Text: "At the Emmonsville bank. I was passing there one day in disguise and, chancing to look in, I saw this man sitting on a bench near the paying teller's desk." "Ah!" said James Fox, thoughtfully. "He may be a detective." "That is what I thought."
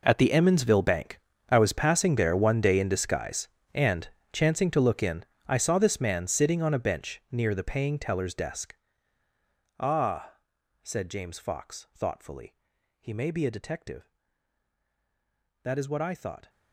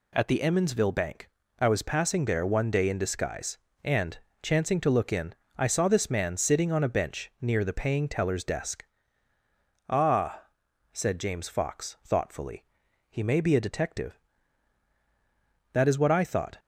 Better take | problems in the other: second | gets quieter; strong; throughout; 17.5 dB

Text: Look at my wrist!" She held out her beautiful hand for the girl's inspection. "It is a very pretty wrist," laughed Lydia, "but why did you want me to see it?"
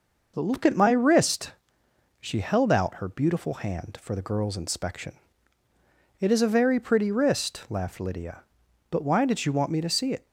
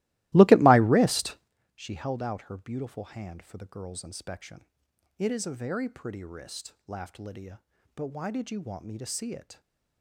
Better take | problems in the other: first | starts louder than the rest; strong; until 1.5 s; 18 dB

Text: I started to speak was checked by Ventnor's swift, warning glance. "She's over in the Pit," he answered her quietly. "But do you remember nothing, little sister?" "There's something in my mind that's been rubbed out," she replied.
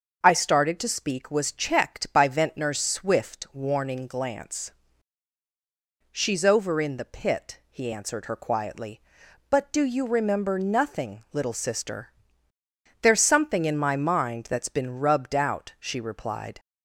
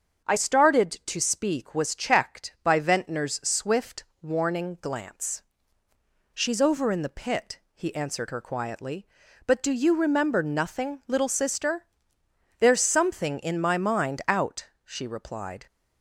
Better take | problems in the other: first | starts louder than the rest; until 1.3 s; 7 dB; also in the first // skips "that's been rubbed"; at 14.2 s

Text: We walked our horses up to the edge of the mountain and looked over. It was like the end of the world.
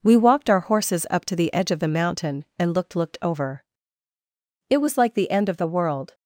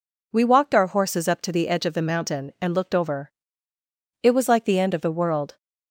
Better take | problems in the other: second | says "looked" twice; at 2.9 s

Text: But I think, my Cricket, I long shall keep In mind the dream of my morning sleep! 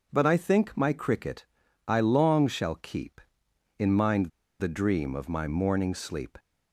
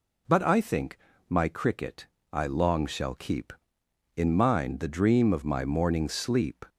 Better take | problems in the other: second | pauses between "mind" and "the"; slight; at 4.3 s; 0.30 s long

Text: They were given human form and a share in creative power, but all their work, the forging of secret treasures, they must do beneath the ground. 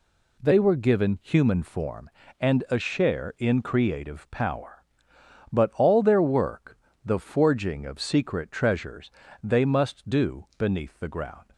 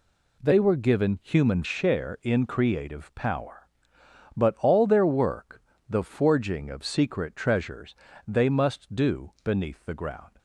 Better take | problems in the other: first | skips "form and a"; at 1.6 s

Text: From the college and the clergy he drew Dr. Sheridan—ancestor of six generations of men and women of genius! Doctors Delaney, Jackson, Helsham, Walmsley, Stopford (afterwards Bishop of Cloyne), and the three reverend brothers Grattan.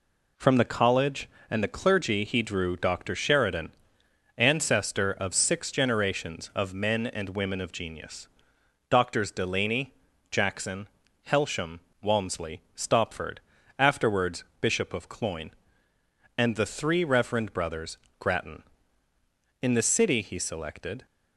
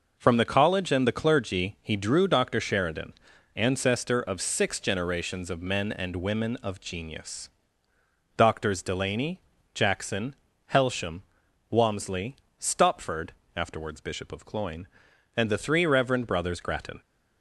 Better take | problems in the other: second | pauses between "afterwards" and "Bishop"; slight; at 14.4 s; 0.16 s long // pauses between "brothers" and "Grattan"; slight; at 17.9 s; 0.24 s long // goes on to say "In the city he selected"; from 19.6 s on; 1.4 s long

